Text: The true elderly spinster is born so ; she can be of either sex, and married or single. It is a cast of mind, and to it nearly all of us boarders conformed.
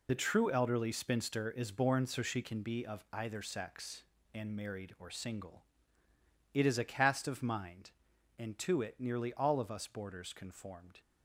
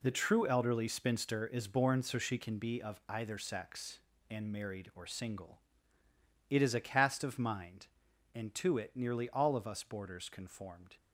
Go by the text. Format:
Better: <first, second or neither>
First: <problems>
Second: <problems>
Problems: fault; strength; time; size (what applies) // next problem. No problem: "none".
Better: second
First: loses the start of "The"; at 0.0 s; 30 ms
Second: none